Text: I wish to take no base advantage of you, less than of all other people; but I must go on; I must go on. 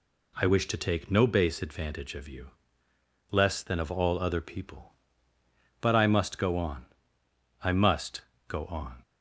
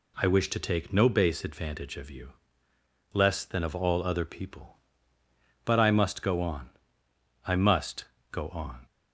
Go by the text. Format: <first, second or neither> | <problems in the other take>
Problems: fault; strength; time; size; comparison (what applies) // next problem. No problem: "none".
neither | pauses between "must" and "go"; slight; the same in both